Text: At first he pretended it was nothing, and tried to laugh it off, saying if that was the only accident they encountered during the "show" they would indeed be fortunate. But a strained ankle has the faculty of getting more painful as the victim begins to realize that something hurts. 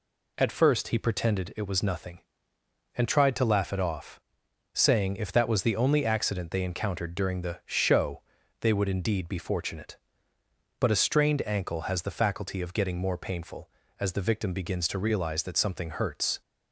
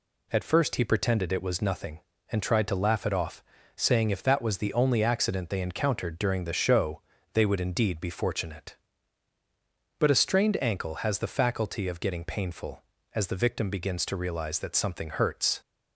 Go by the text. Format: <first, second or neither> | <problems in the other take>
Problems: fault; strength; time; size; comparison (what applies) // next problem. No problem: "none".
first | pauses between "show" and "they"; slight; at 7.0 s; 0.32 s long; also in the first // skips "more"; at 12.2 s